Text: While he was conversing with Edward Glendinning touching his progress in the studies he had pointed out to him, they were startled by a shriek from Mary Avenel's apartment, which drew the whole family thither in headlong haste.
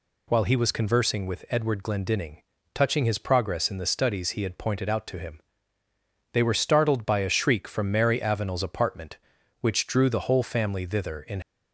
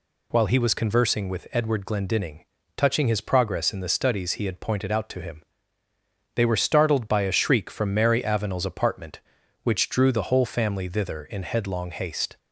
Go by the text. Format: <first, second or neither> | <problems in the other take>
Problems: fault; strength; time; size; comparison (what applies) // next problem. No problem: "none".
second | pauses between "Glendinning" and "touching"; slight; at 2.4 s; 0.32 s long; slight in the second // stops before "headlong haste"; at 11.4 s